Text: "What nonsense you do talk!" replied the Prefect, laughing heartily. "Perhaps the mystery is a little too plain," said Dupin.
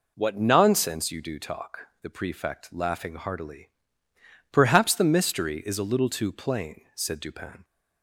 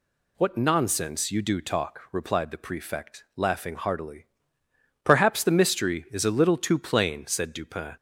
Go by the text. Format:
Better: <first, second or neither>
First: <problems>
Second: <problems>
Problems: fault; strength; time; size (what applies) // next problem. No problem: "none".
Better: second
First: skips "replied"; at 1.9 s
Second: none